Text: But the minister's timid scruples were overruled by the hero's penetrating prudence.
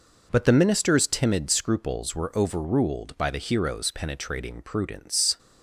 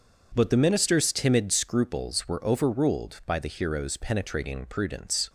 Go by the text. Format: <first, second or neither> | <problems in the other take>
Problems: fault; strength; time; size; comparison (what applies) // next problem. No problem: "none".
neither | none